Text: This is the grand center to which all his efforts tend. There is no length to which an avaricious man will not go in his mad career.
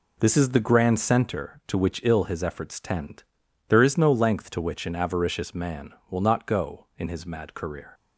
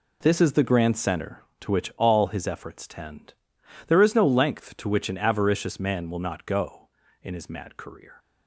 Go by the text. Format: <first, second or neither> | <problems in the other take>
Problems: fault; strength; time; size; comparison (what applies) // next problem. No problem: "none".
second | says "ill" for "all"; at 2.0 s